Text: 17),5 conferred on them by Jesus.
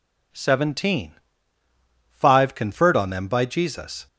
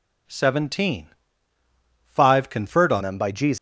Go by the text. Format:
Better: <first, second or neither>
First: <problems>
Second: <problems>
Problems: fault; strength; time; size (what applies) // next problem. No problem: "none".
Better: first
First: none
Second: changes voice at "them"; from 3.0 s on; 0.5 s long